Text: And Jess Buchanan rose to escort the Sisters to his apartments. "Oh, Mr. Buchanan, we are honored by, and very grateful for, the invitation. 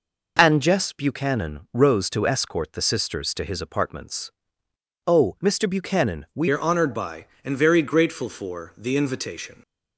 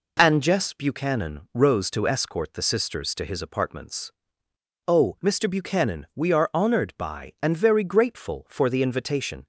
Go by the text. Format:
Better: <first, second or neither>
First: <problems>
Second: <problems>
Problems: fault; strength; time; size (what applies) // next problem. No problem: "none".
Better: second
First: changes voice at "are"; from 6.4 s on; 3.2 s long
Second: none